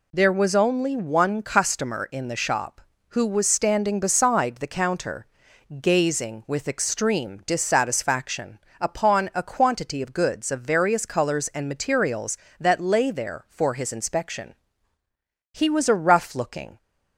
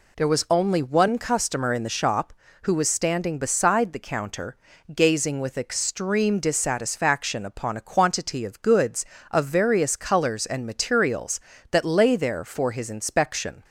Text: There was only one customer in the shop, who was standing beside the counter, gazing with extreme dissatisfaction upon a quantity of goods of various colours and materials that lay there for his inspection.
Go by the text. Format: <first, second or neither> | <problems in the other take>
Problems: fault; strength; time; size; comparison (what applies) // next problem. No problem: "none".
second | pauses between "dissatisfaction" and "upon"; slight; at 8.5 s; 0.22 s long // goes on to say "He was a rough looking"; noticeable; from 15.5 s on; 1.2 s long